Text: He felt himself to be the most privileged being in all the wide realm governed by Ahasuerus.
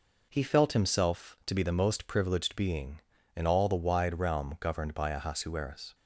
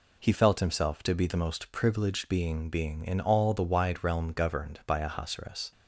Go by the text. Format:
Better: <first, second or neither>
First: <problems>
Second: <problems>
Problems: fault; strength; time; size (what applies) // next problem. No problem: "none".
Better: first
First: none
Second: says "being" twice; at 2.6 s